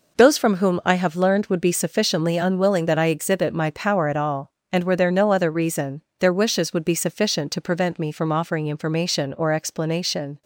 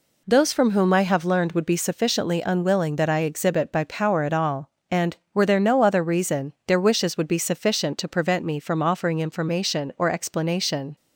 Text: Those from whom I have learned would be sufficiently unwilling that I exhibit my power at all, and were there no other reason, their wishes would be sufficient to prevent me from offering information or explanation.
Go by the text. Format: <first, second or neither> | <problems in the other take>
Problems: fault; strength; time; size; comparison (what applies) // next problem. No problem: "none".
first | says "by" for "my"; at 3.7 s